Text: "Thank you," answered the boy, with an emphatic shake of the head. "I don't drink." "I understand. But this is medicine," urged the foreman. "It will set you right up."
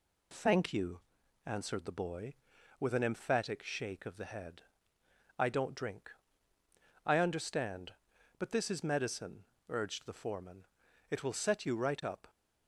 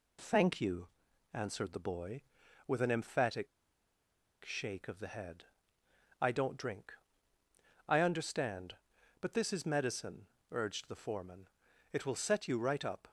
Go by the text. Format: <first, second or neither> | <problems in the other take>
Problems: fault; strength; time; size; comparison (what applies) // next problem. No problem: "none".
first | pauses between "emphatic" and "shake"; noticeable; at 3.4 s; 0.97 s long